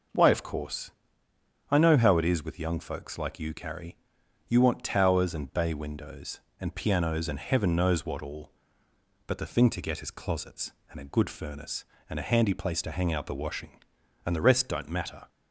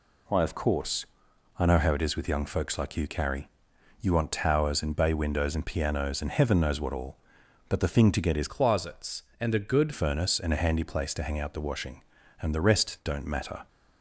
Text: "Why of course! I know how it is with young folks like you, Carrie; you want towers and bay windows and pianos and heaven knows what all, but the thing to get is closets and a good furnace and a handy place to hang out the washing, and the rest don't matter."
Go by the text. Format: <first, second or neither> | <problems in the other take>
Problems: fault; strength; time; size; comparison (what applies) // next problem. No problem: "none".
first | changes voice from "closets" to "good"; from 8.4 to 9.9 s; 1.5 s long